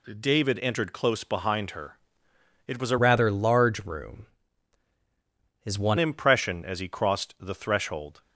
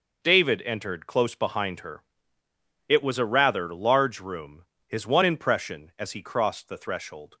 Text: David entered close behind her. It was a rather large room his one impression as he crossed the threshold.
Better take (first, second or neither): second